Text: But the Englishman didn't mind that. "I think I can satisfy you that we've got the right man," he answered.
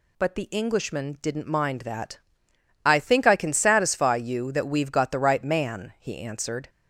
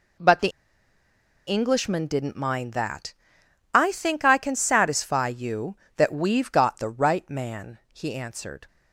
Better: first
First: none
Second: pauses between "the" and "Englishman"; noticeable; at 0.4 s; 0.98 s long

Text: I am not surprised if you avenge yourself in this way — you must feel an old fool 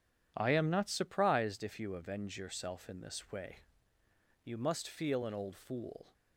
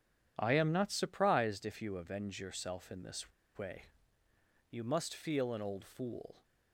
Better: first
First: none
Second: pauses between "this" and "way"; slight; at 3.3 s; 0.25 s long

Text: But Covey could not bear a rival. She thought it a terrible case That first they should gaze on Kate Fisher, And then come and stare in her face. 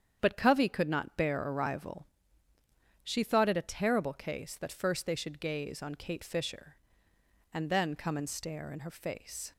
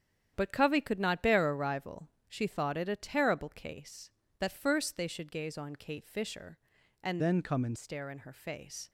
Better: first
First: starts louder than the rest; strong; until 1.2 s; 8 dB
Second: starts louder than the rest; strong; until 1.3 s; 9 dB // changes voice from "then" to "and"; from 7.1 to 7.7 s; 0.6 s long

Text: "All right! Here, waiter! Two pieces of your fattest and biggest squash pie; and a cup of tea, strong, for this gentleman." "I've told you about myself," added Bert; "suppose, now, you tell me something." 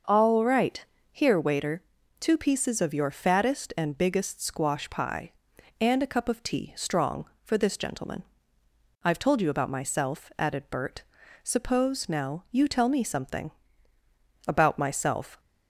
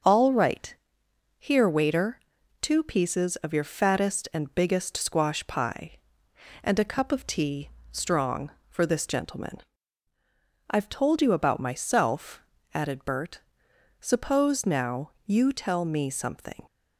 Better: second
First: starts louder than the rest; until 1.3 s; 6 dB // goes on to say "About myself"; noticeable; from 14.4 s on; 0.94 s long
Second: starts louder than the rest; until 1.6 s; 6.5 dB

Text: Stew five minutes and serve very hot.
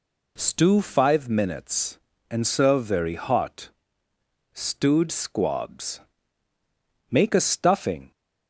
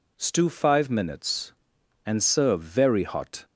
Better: second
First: goes on to say "Stewed Squabs Make a stuffing"; strong; from 4.5 s on; 3.5 s long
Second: none

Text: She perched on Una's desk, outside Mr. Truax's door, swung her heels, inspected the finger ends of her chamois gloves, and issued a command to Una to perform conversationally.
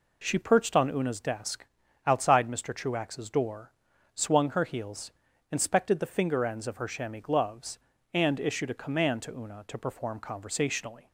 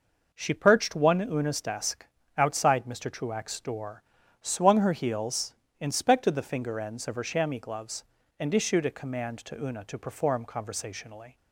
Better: first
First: none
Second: says "one" for "on"; at 0.9 s

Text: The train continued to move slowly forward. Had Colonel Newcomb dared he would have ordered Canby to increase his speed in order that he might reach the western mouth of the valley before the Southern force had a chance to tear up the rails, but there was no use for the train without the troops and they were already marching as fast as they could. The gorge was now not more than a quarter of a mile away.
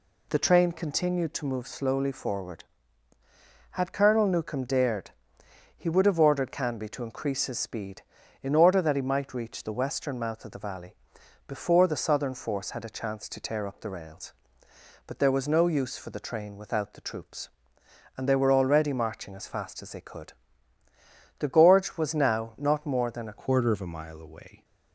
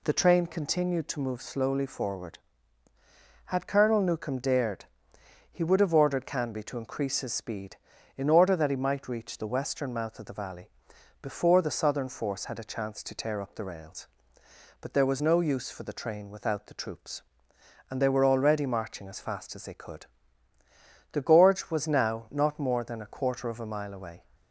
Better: second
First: pauses between "dared" and "he"; noticeable; at 5.1 s; 0.64 s long // pauses between "valley" and "before"; noticeable; at 10.9 s; 0.52 s long // changes voice at "quarter"; from 23.3 s on; 1.3 s long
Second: pauses between "dared" and "he"; noticeable; at 4.8 s; 0.64 s long // pauses between "valley" and "before"; noticeable; at 10.6 s; 0.52 s long

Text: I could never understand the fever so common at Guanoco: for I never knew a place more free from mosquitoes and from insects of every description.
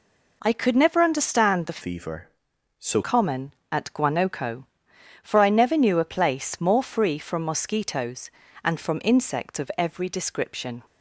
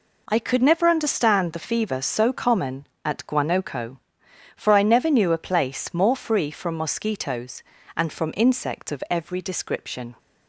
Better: second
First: changes voice from "fever" to "so"; from 1.8 to 3.0 s; 1.2 s long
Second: none

